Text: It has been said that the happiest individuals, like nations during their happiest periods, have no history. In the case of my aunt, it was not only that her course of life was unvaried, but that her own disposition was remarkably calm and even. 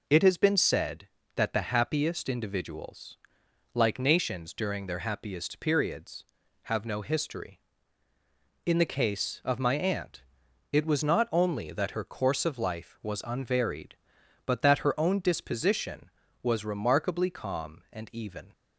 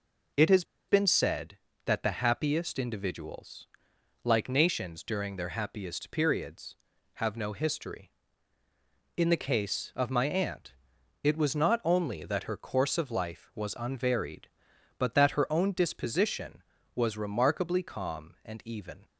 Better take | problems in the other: first | pauses between "has" and "been"; slight; at 0.6 s; 0.25 s long

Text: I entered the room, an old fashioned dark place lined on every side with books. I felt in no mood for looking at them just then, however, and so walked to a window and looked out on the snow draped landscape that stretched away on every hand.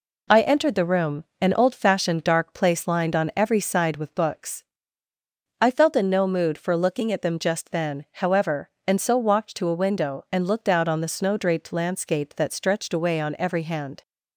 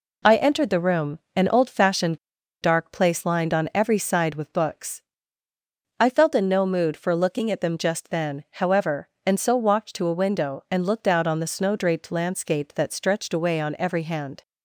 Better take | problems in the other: first | pauses between "fashioned" and "dark"; at 2.1 s; 0.45 s long

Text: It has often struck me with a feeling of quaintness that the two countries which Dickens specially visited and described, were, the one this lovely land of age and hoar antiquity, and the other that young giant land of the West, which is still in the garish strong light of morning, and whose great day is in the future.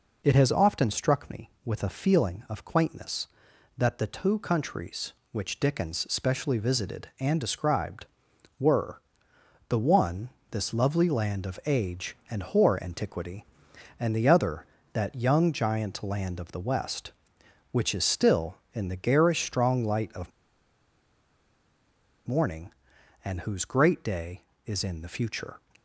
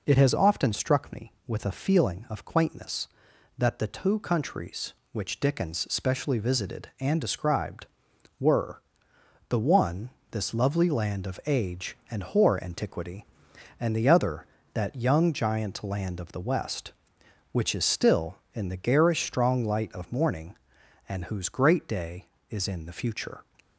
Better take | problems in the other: second | pauses between "one" and "this"; slight; at 10.3 s; 0.20 s long; slight in the second // pauses between "of" and "morning"; strong; at 20.3 s; 1.9 s long

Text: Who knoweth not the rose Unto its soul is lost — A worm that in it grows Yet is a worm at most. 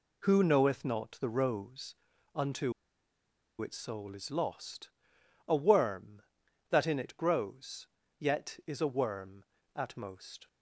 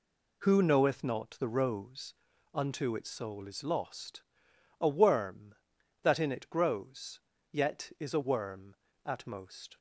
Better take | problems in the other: second | pauses between "rose" and "Unto"; at 1.9 s; 0.40 s long; also in the second // pauses between "Unto" and "its"; noticeable; at 2.7 s; 0.88 s long // pauses between "grows" and "Yet"; slight; at 7.8 s; 0.32 s long; slight in the second

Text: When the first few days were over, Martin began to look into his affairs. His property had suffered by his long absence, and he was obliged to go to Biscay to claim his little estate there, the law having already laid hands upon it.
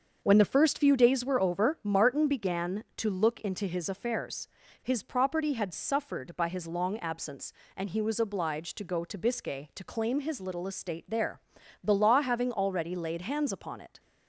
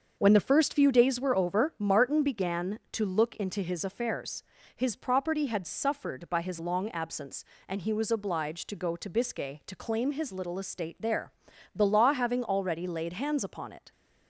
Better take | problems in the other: neither | starts louder than the rest; the same in both

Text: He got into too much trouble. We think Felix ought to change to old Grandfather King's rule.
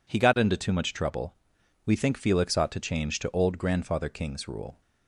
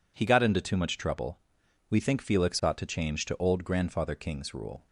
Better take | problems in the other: neither | none

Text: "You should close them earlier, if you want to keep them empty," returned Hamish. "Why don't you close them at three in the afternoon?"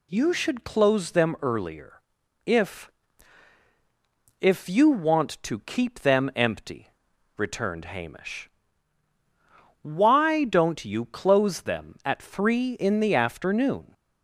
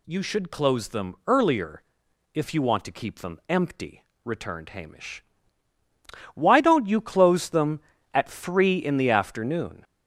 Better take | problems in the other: second | says "if" twice; at 4.4 s

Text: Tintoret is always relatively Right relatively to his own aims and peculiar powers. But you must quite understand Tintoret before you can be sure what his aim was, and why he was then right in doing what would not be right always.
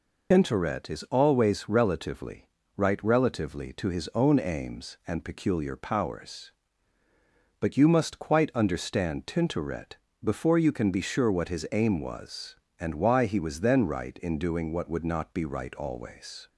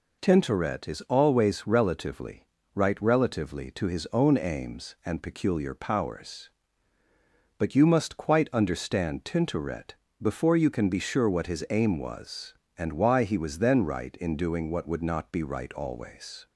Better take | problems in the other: second | loses the start of "Tintoret"; at 0.3 s; 80 ms // pauses between "relatively" and "Right"; slight; at 2.4 s; 0.30 s long; slight in the second // pauses between "Tintoret" and "before"; slight; at 9.9 s; 0.28 s long; slight in the second

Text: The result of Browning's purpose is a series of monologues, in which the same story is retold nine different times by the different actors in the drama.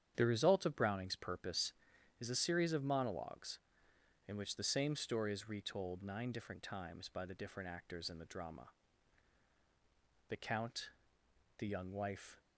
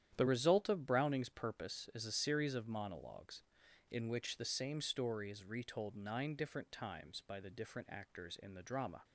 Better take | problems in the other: second | starts louder than the rest; strong; until 1.1 s; 9 dB; strong in the second // goes on to say "The count the young wife"; strong; from 10.2 s on; 2.0 s long

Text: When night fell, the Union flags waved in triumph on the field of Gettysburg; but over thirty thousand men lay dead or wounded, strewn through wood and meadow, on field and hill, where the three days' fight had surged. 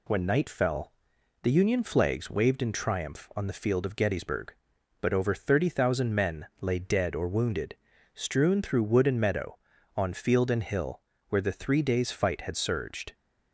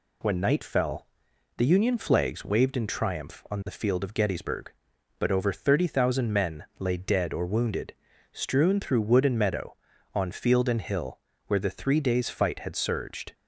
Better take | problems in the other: neither | pauses between "men" and "lay"; slight; the same in both

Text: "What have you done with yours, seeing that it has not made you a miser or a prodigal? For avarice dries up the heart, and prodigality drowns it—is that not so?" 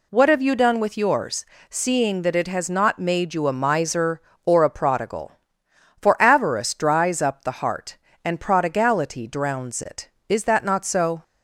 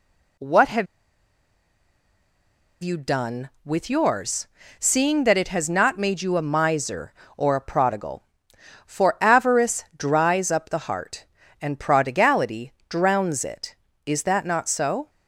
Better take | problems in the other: first | pauses between "have" and "you"; strong; at 0.8 s; 1.9 s long // pauses between "prodigality" and "drowns"; slight; at 12.7 s; 0.18 s long

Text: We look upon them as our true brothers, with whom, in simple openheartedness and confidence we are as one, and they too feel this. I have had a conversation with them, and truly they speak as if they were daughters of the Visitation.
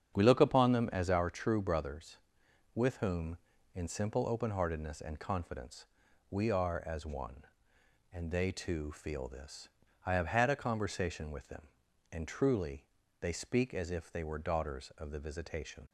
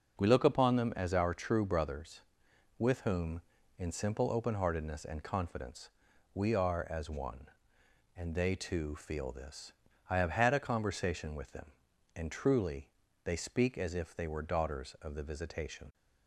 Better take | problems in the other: second | starts louder than the rest; strong; until 1.3 s; 8 dB // pauses between "confidence" and "we"; noticeable; at 5.8 s; 0.46 s long; noticeable in the second // pauses between "truly" and "they"; slight; at 12.8 s; 0.36 s long; slight in the second

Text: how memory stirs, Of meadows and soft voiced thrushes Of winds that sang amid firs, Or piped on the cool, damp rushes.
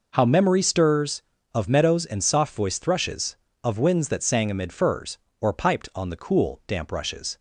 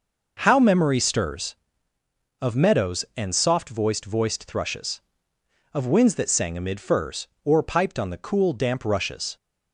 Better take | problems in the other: first | says "voiced" twice; at 4.0 s

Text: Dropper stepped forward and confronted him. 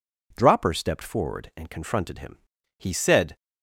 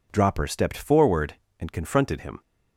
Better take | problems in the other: second | goes on to say "He said"; from 2.7 s on; 0.58 s long

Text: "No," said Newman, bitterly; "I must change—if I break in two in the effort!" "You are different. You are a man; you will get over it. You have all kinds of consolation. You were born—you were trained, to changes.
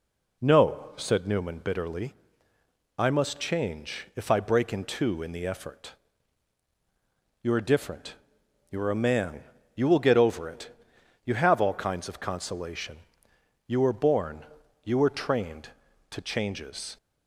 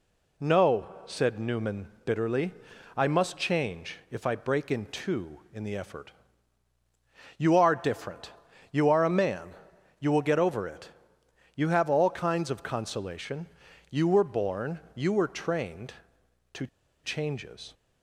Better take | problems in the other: first | pauses between "to" and "changes"; at 16.6 s; 0.36 s long

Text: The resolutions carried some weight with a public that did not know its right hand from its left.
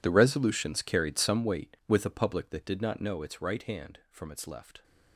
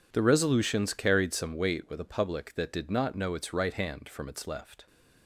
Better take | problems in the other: second | gets quieter; strong; throughout; 18.5 dB

